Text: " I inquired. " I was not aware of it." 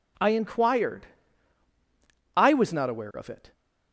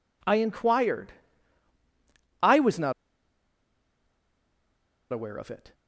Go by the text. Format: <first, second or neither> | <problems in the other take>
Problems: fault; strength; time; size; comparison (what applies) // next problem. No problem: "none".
first | pauses between "not" and "aware"; strong; at 2.9 s; 2.1 s long